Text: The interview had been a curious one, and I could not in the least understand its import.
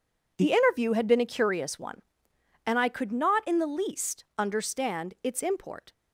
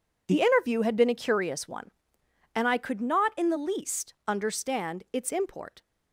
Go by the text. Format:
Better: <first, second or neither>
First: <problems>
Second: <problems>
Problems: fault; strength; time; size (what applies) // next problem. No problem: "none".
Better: neither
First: none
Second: none